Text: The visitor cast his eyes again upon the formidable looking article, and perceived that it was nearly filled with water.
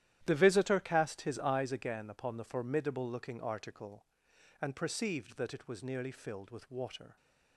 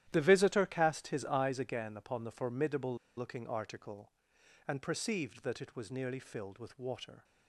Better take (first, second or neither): first